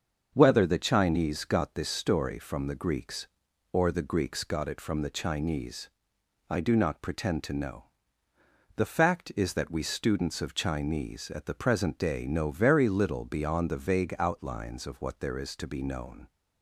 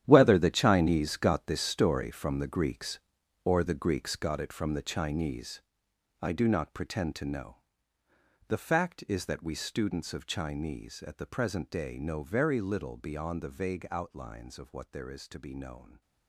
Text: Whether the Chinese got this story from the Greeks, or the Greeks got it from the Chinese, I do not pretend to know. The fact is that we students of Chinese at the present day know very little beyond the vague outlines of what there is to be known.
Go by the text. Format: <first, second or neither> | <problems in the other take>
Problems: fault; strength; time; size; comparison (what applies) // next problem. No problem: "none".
first | gets quieter; strong; throughout; 13 dB // starts louder than the rest; strong; until 1.0 s; 10.5 dB; also in the first